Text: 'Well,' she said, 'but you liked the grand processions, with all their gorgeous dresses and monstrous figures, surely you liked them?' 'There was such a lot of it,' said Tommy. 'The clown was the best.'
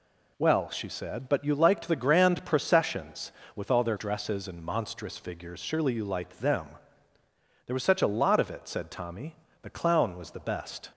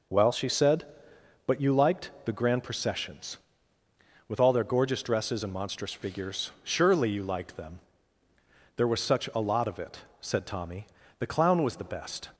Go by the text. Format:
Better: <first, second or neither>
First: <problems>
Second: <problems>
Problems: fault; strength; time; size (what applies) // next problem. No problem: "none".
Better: second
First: skips "gorgeous"; at 3.9 s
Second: none